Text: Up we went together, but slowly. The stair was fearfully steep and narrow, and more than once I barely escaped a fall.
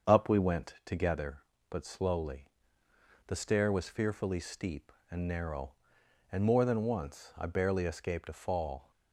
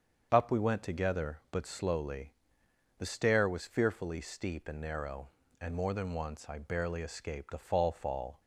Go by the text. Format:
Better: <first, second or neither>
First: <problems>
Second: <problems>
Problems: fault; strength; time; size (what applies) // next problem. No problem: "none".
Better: first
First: starts louder than the rest; until 1.1 s; 7 dB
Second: starts louder than the rest; until 1.3 s; 7 dB // says "fall" twice; at 7.9 s